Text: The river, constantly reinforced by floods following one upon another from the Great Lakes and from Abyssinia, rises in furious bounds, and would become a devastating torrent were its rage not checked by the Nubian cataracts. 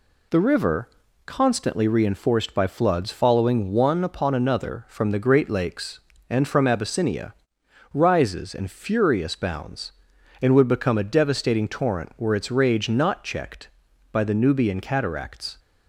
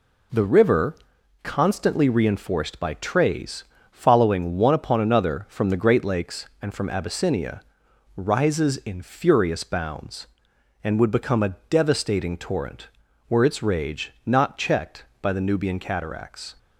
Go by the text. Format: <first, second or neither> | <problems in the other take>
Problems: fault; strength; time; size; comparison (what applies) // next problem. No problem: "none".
first | says "trays" for "floods"; at 2.9 s